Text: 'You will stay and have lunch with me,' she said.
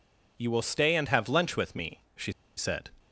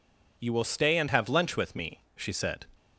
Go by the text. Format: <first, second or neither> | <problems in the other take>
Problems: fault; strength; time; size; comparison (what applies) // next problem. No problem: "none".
second | pauses between "she" and "said"; slight; at 2.3 s; 0.24 s long